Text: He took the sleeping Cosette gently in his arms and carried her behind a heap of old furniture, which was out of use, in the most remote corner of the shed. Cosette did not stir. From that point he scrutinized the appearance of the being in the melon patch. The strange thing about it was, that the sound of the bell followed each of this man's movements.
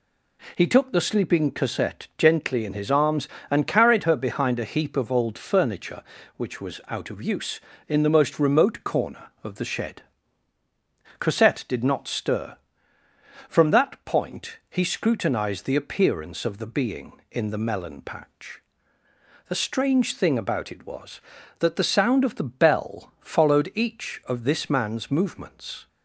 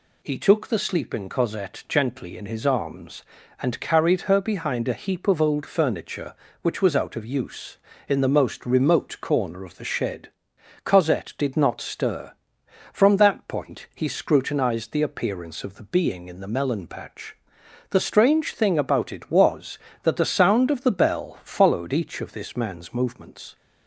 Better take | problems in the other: neither | none

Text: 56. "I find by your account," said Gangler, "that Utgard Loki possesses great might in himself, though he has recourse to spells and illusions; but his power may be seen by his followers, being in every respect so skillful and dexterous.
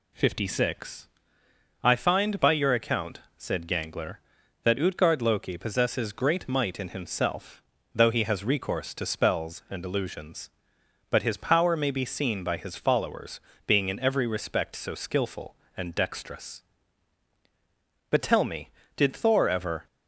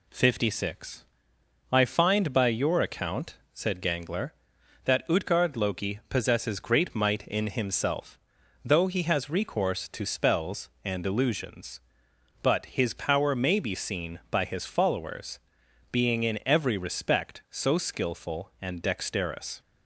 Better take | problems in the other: second | goes on to say "But tell me did Thor ever"; strong; from 18.1 s on; 1.7 s long

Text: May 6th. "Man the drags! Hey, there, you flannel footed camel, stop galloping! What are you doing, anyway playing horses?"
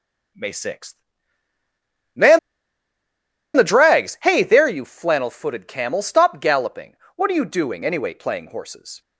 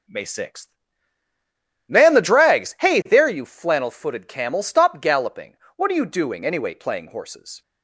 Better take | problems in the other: second | pauses between "Man" and "the"; at 2.3 s; 1.1 s long

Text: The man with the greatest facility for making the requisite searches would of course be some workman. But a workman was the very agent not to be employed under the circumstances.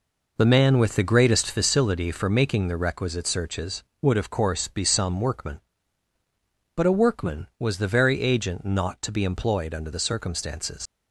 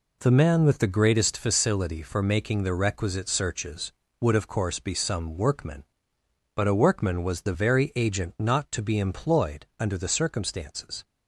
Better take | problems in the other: second | leaves "circumstances" unfinished; at 10.8 s; 105 ms

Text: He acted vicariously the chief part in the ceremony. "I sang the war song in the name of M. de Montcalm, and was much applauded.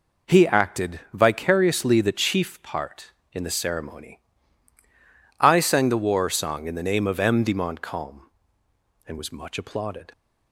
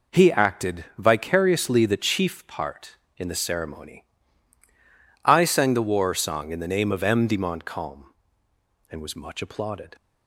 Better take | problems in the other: neither | none

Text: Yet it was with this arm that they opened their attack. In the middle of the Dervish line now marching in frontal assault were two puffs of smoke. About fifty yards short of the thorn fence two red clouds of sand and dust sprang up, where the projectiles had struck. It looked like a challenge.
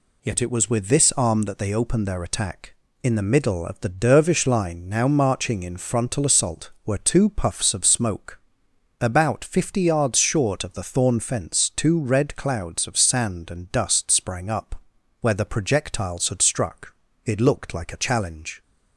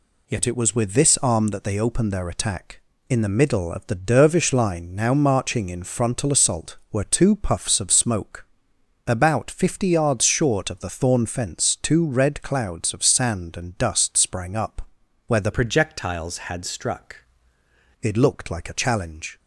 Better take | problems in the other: first | changes voice from "projectiles" to "struck"; from 15.5 to 17.1 s; 1.6 s long

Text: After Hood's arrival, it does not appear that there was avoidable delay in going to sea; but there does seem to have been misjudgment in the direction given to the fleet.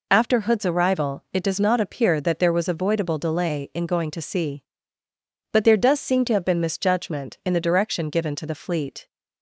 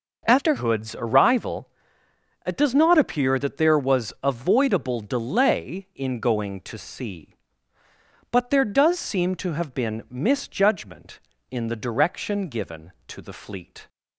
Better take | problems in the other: first | changes voice at "Hood's"; from 0.5 s on; 13.3 s long

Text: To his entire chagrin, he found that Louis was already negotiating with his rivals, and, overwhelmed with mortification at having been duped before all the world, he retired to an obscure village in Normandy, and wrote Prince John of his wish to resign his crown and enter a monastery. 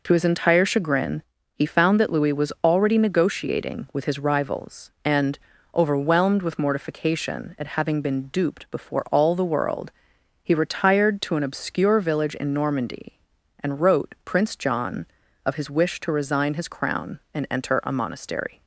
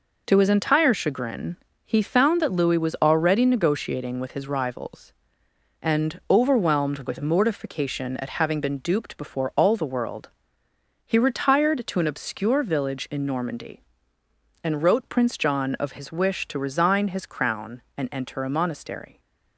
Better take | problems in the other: neither | none

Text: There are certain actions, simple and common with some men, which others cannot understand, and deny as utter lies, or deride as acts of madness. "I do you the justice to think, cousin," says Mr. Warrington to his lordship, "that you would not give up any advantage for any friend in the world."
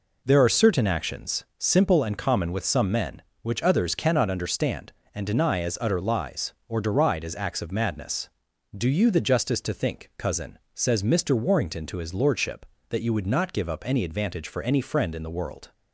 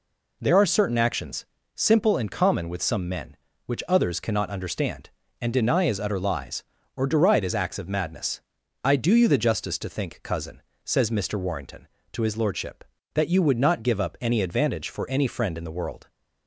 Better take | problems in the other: second | skips "I"; at 8.5 s

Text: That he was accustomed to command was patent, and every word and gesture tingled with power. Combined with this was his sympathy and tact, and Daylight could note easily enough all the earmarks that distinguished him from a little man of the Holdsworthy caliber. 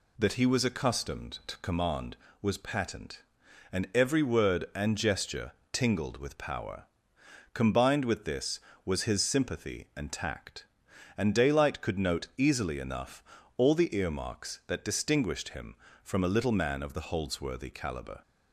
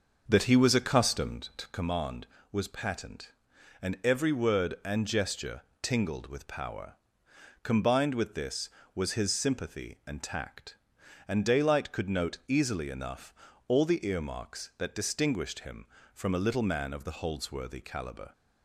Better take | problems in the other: first | starts louder than the rest; until 1.5 s; 6.5 dB // pauses between "gesture" and "tingled"; slight; at 5.6 s; 0.20 s long; slight in the first // pauses between "enough" and "all"; slight; at 13.3 s; 0.36 s long; slight in the first

